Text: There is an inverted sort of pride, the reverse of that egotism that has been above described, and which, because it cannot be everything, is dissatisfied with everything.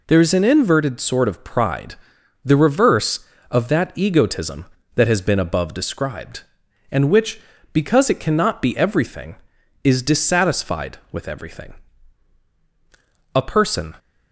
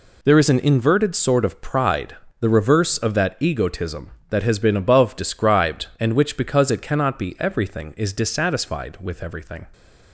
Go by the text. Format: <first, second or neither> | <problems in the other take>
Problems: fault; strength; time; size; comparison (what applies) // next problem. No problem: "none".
second | goes on to say "A person"; noticeable; from 13.3 s on; 0.62 s long